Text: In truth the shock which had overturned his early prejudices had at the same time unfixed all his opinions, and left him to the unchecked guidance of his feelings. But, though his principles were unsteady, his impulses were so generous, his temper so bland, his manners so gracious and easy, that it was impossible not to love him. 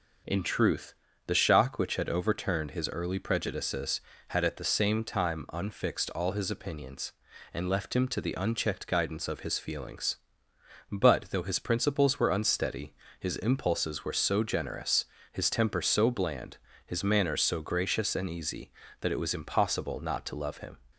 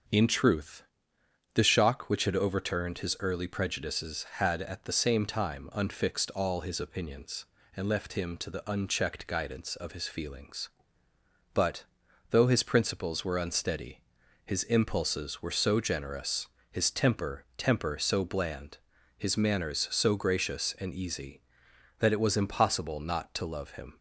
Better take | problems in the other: first | starts louder than the rest; until 1.8 s; 6.5 dB // pauses between "truth" and "the"; noticeable; at 0.8 s; 0.72 s long; slight in the first // says "temper" twice; at 17.5 s

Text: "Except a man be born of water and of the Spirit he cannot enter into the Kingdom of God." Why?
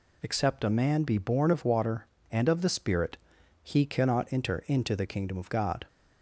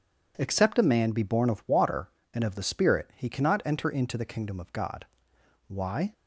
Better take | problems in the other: second | pauses between "Spirit" and "he"; at 3.1 s; 0.44 s long // stops before "Why"; at 5.8 s

